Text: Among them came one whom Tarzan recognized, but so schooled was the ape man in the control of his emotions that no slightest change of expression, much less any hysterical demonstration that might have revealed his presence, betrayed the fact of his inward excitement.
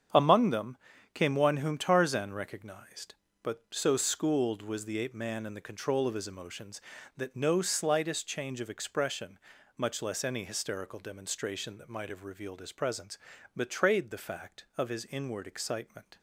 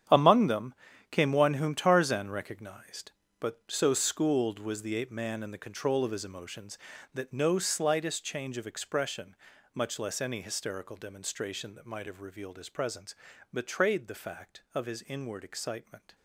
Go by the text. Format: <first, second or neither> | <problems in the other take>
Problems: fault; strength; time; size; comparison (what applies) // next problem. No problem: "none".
first | gets quieter; strong; throughout; 13 dB // starts louder than the rest; strong; until 1.4 s; 9.5 dB; strong in the first // pauses between "them" and "came"; at 0.7 s; 0.38 s long; also in the first